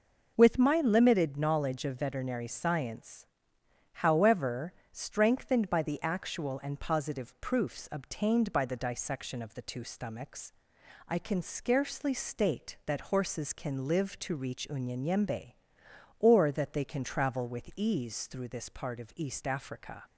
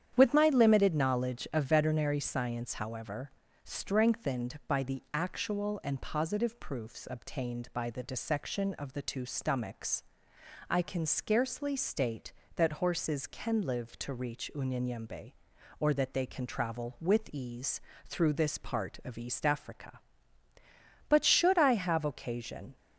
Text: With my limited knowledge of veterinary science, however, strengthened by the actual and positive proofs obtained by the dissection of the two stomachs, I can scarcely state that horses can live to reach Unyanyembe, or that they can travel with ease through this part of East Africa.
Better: first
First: none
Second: starts louder than the rest; strong; until 1.1 s; 9.5 dB // pauses between "ease" and "through"; slight; at 17.7 s; 0.26 s long // goes on to say "But should I have occasion"; strong; from 21.0 s on; 1.6 s long

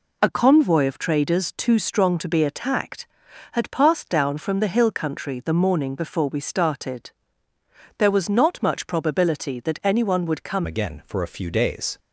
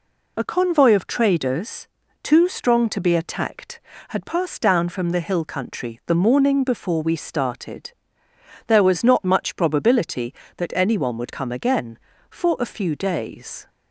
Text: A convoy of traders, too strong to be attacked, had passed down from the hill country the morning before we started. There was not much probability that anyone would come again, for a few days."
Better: second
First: changes voice at "again"; from 10.6 s on; 1.3 s long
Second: none

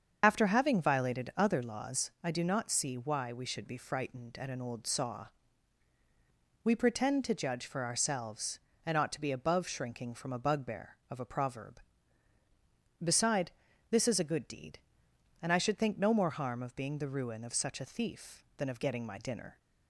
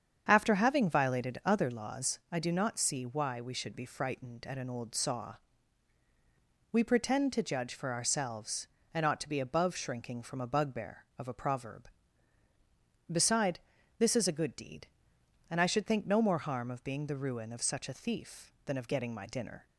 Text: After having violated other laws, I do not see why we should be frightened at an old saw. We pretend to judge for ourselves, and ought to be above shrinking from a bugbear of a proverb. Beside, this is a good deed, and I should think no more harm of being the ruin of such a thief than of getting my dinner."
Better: second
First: loses the start of "After"; at 0.2 s; 55 ms // starts louder than the rest; until 1.2 s; 7 dB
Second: starts louder than the rest; strong; until 1.3 s; 7.5 dB

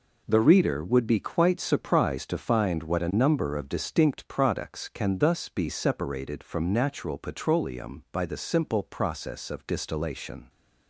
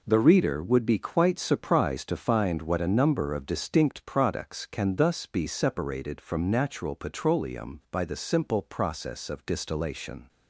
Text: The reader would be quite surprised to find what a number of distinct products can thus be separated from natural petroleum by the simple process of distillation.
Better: neither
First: none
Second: none

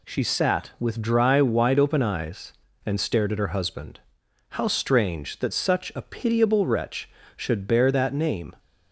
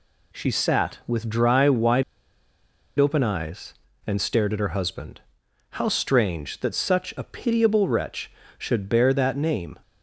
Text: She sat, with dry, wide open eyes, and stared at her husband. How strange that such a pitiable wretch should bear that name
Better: first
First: none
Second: pauses between "wide" and "open"; noticeable; at 2.0 s; 0.96 s long

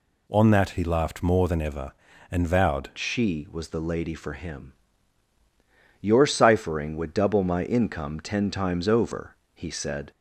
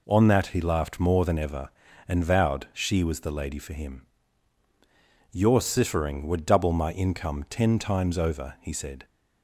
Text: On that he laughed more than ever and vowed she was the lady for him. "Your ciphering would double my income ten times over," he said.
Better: second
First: changes voice at "she"; from 2.9 s on; 7.2 s long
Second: none

